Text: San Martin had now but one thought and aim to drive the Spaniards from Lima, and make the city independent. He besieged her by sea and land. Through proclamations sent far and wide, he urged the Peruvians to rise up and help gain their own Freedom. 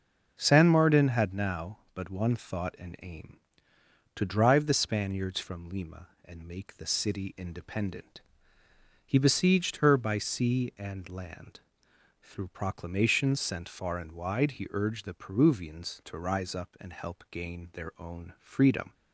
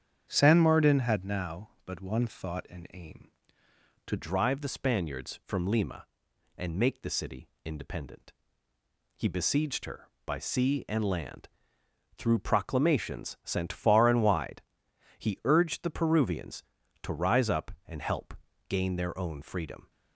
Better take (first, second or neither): first